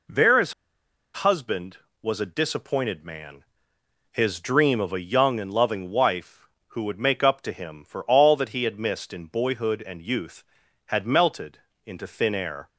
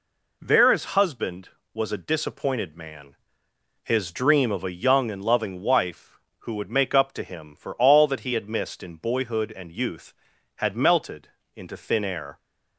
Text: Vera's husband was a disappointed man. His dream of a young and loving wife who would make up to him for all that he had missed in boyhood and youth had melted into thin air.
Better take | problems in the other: second | pauses between "Vera's" and "husband"; noticeable; at 0.5 s; 0.62 s long // pauses between "melted" and "into"; slight; at 11.5 s; 0.28 s long; slight in the second

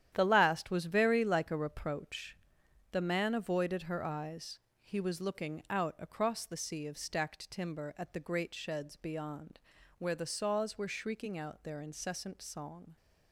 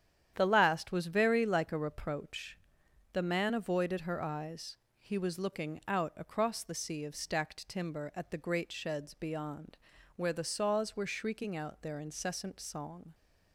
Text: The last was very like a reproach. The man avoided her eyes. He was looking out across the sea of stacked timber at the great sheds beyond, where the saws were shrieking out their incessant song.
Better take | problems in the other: second | gets quieter; strong; throughout; 10 dB // starts louder than the rest; strong; until 1.1 s; 10.5 dB; strong in the second

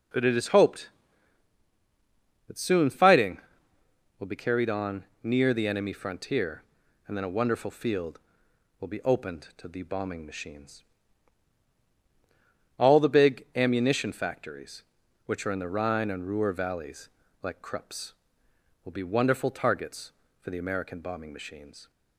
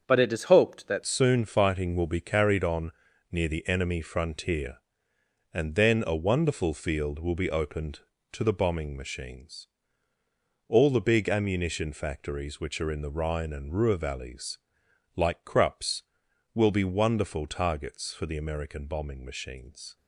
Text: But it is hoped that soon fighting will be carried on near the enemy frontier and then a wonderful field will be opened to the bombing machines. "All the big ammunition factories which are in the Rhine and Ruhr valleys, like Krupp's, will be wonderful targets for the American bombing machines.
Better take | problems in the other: first | starts louder than the rest; strong; until 1.0 s; 7 dB // changes voice at "soon"; from 1.0 s on; 18.9 s long // pauses between "on" and "near"; at 2.9 s; 0.40 s long; slight in the first

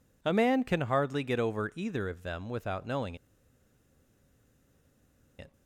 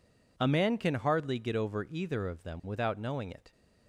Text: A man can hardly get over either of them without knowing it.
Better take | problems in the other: second | pauses between "knowing" and "it"; strong; at 3.1 s; 2.2 s long

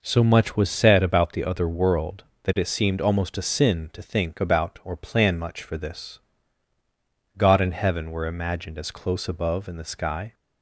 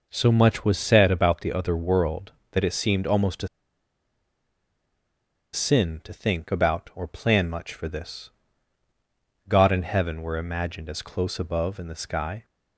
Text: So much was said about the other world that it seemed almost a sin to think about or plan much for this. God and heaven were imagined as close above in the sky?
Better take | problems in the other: first | pauses between "a" and "sin"; strong; at 3.4 s; 2.0 s long

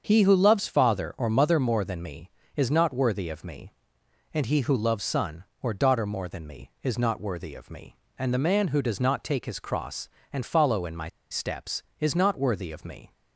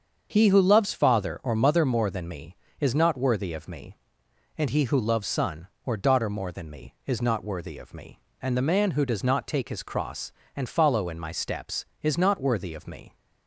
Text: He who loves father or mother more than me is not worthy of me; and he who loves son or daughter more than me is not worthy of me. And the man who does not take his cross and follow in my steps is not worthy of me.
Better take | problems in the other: second | starts louder than the rest; until 1.1 s; 7 dB; also in the second // pauses between "my" and "steps"; slight; at 11.0 s; 0.23 s long

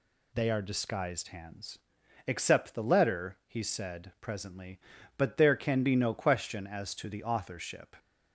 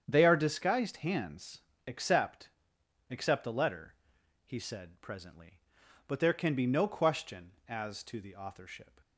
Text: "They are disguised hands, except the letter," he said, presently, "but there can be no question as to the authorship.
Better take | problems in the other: first | starts louder than the rest; strong; until 1.0 s; 8 dB // says "except" twice; at 3.0 s

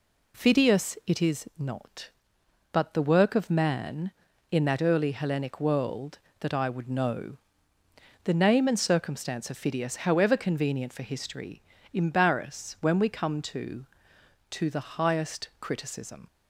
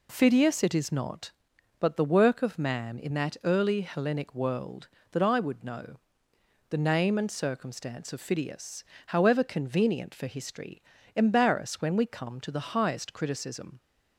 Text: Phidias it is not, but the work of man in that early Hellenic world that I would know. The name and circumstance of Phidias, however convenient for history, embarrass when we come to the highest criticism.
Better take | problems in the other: second | says "to" twice; at 14.5 s

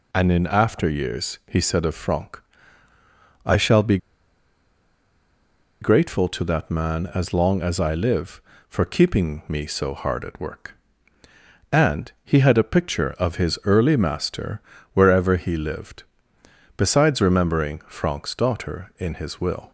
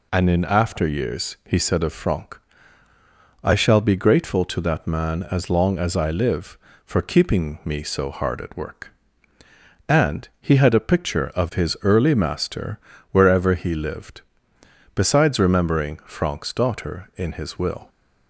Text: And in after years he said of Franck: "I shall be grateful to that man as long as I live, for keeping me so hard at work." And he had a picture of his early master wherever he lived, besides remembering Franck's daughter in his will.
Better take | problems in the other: second | pauses between "be" and "grateful"; strong; at 3.9 s; 1.8 s long // pauses between "master" and "wherever"; slight; at 14.6 s; 0.34 s long; slight in the second

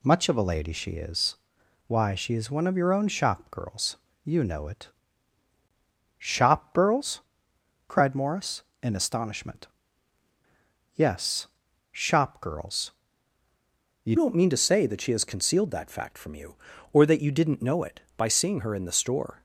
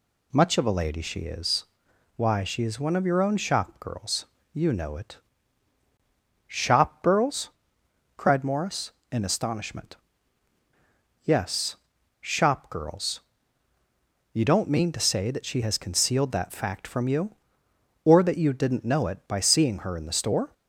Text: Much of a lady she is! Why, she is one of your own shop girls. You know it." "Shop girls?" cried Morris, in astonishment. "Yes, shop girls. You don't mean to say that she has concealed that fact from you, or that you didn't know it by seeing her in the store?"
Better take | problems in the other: second | changes voice at "don't"; from 14.1 s on; 5.3 s long

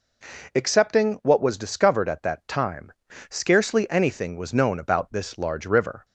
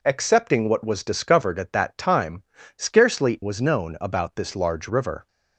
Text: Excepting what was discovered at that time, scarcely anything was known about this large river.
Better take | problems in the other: first | skips "anything"; at 3.4 s

